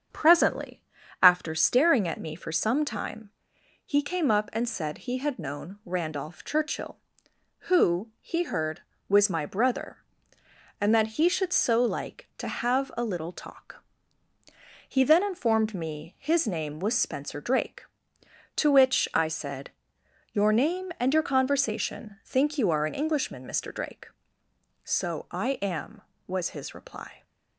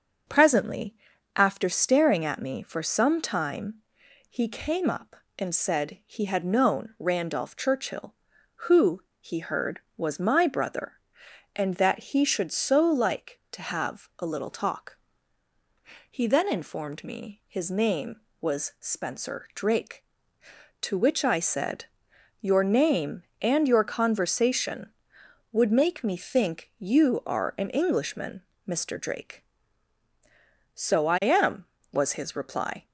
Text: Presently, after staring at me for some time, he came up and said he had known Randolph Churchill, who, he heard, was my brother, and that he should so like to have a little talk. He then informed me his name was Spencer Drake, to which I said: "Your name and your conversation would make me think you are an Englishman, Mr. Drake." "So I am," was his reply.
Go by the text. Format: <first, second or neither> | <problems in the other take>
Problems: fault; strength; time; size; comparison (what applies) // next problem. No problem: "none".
second | starts louder than the rest; until 1.5 s; 7 dB; also in the second // skips "would make me"; at 22.2 s